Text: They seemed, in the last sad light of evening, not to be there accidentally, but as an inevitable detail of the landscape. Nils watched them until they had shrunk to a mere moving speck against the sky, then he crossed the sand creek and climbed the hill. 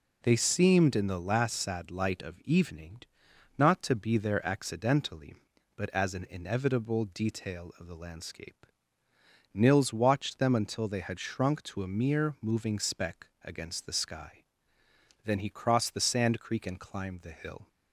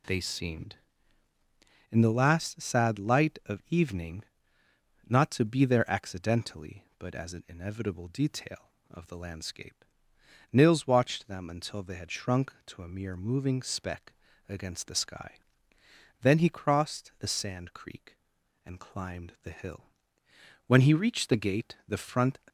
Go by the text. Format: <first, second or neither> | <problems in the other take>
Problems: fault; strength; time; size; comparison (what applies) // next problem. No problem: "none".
first | pauses between "speck" and "against"; slight; at 14.1 s; 0.34 s long; slight in the first // goes on to say "When he reached the gate the front"; strong; from 20.6 s on; 1.7 s long